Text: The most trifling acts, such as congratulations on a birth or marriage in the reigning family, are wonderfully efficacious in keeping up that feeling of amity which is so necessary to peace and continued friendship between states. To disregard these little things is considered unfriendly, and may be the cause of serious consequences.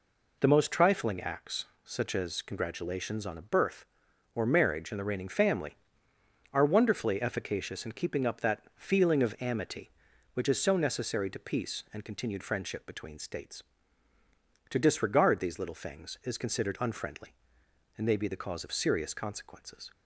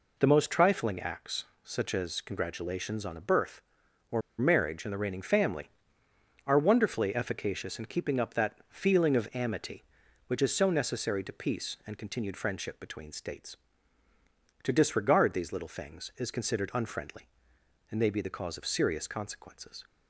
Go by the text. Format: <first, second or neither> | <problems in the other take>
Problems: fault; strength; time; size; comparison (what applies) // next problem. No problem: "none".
first | pauses between "or" and "marriage"; slight; at 4.2 s; 0.19 s long